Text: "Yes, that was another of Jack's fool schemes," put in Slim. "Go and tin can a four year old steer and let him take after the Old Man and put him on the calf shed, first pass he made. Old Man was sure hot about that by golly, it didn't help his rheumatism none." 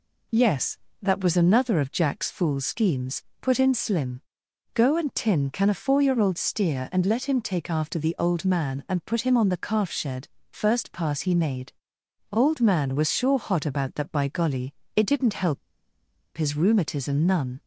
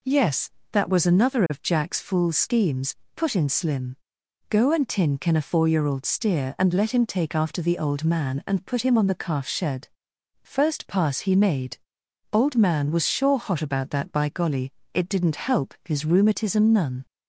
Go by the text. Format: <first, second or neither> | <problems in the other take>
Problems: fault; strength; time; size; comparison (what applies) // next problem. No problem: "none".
second | pauses between "help" and "his"; noticeable; at 15.5 s; 0.78 s long